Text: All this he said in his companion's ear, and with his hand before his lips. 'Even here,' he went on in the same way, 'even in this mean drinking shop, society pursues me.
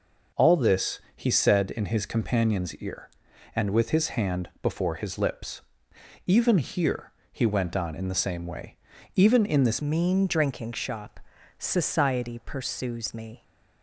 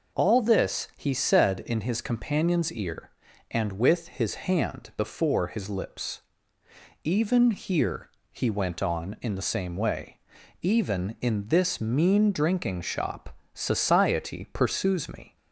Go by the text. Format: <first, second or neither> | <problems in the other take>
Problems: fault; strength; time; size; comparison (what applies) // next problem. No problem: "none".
second | pauses between "this" and "he"; slight; at 0.9 s; 0.16 s long // changes voice at "mean"; from 9.8 s on; 3.6 s long